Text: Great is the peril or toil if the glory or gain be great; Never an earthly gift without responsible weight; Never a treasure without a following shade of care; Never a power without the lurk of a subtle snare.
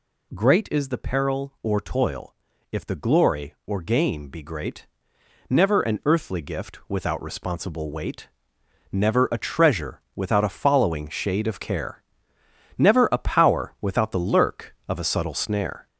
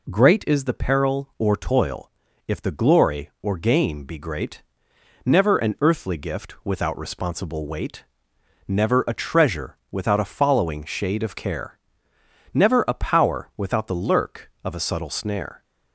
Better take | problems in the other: second | gets louder; noticeable; throughout; 4 dB // pauses between "toil" and "if"; slight; at 2.3 s; 0.36 s long; slight in the second

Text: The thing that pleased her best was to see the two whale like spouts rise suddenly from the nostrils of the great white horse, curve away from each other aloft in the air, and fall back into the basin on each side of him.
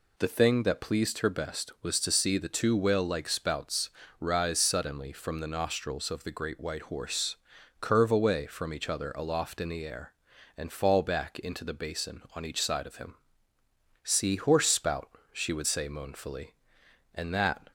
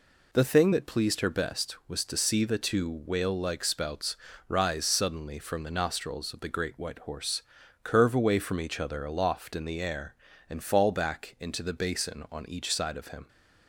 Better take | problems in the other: second | pauses between "spouts" and "rise"; slight; at 3.9 s; 0.28 s long; slight in the second // goes on to say "See horse spout she would say moanfully and that"; strong; from 14.0 s on; 3.6 s long

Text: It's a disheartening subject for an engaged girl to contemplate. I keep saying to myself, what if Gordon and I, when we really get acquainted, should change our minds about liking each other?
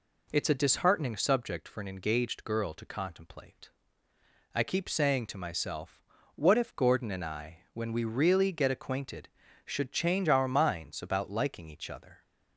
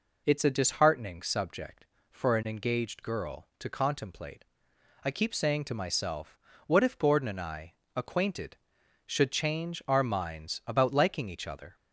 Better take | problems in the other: first | skips "when we really get"; at 7.8 s

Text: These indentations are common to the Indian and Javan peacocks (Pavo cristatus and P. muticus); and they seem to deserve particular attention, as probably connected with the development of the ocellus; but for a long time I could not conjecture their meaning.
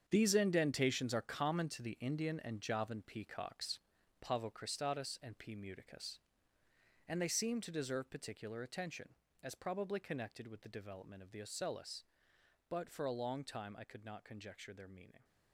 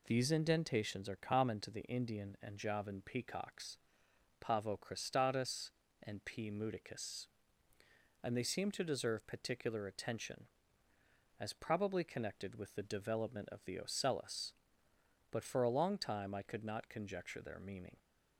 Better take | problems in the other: second | gets quieter; strong; throughout; 11.5 dB

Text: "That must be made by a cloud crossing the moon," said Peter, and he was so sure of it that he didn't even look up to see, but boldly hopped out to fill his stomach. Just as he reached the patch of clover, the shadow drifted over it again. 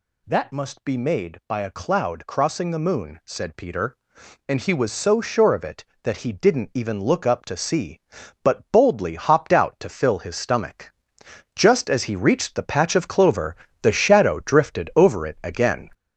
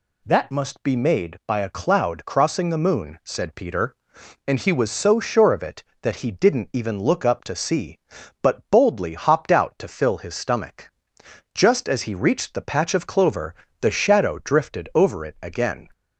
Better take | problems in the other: second | gets louder; throughout; 6.5 dB

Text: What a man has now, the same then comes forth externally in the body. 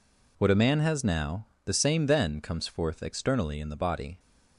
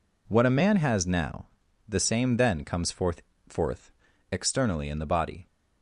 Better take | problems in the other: first | says "forth" twice; at 3.4 s

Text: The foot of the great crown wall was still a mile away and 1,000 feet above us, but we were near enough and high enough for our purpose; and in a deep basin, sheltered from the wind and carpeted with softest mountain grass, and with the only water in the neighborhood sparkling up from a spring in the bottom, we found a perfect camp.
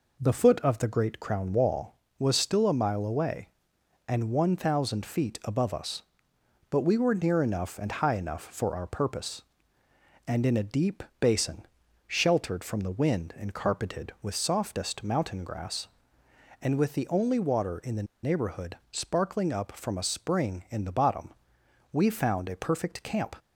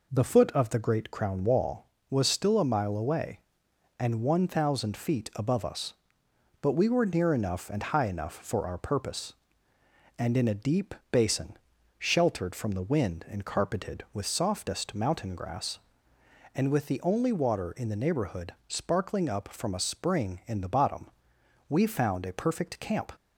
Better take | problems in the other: second | pauses between "deep" and "basin"; slight; at 11.0 s; 0.16 s long; slight in the second // pauses between "the" and "neighborhood"; slight; at 18.0 s; 0.19 s long // pauses between "neighborhood" and "sparkling"; slight; at 18.7 s; 0.16 s long; slight in the second

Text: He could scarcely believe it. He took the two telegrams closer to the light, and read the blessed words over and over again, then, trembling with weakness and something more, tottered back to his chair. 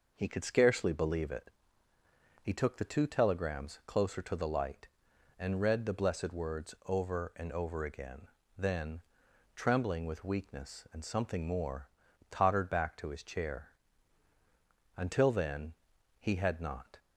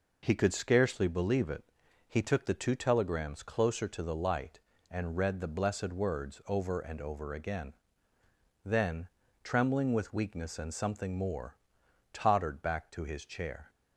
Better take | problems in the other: second | goes on to say "Until then he had not"; strong; from 14.9 s on; 2.0 s long

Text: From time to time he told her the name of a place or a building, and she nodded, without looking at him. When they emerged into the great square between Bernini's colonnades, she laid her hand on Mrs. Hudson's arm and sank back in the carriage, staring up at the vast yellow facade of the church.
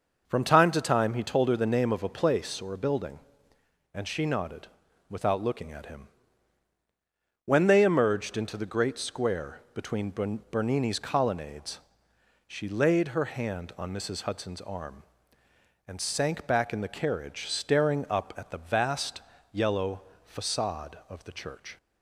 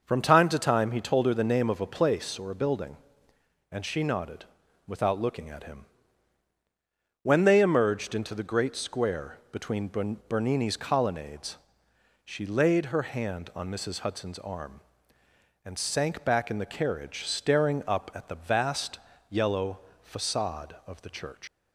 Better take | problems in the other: first | starts louder than the rest; noticeable; until 1.0 s; 6 dB; noticeable in the first // pauses between "vast" and "yellow"; slight; at 18.9 s; 0.32 s long; slight in the first // pauses between "yellow" and "facade"; slight; at 19.7 s; 0.24 s long; slight in the first // leaves "church" unfinished; at 21.4 s; 70 ms

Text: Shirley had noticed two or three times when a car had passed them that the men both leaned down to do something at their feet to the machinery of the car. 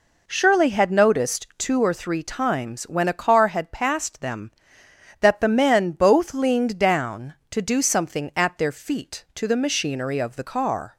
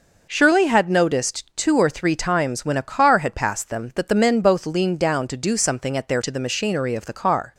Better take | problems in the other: first | skips "feet"; at 6.2 s

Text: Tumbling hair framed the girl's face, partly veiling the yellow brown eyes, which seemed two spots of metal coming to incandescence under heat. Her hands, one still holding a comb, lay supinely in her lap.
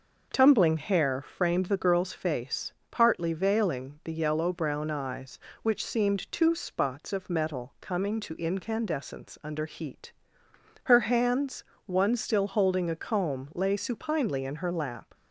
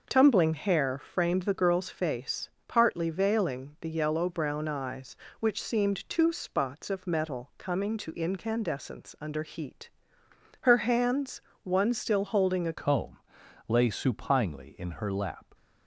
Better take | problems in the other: first | changes voice at "comb"; from 12.7 s on; 2.7 s long

